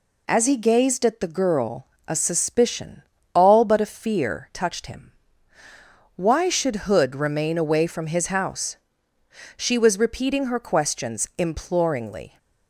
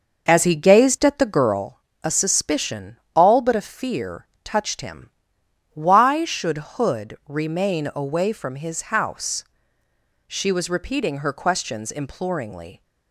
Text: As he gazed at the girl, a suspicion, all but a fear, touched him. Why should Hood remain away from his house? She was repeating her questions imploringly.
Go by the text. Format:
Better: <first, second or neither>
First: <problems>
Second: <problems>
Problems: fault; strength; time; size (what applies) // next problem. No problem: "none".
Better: first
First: none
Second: starts louder than the rest; noticeable; until 1.6 s; 6 dB // pauses between "should" and "Hood"; slight; at 6.5 s; 0.16 s long